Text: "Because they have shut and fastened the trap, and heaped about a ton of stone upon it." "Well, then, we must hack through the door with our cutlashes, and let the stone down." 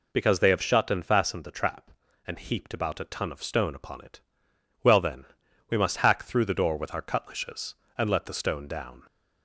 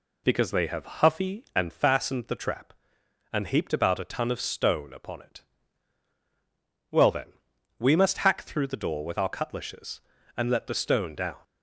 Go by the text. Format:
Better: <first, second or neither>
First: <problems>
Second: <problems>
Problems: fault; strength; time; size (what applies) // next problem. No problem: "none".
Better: first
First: none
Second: says "huffy" for "shut"; at 0.8 s